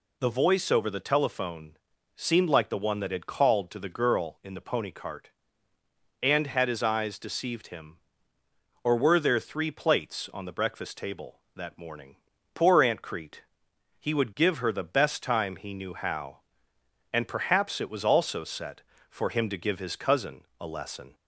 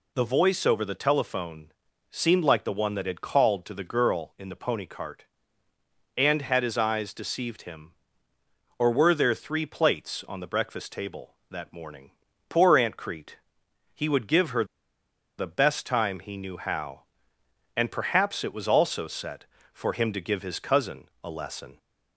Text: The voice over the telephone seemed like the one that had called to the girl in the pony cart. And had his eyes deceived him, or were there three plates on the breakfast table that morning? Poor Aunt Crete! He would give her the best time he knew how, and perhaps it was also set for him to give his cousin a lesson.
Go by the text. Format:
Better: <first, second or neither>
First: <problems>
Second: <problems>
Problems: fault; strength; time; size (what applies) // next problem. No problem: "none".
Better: first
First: pauses between "telephone" and "seemed"; at 1.7 s; 0.40 s long // pauses between "cousin" and "a"; slight; at 20.4 s; 0.18 s long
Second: pauses between "telephone" and "seemed"; at 1.7 s; 0.40 s long // pauses between "her" and "the"; noticeable; at 14.6 s; 0.74 s long // pauses between "cousin" and "a"; slight; at 21.0 s; 0.18 s long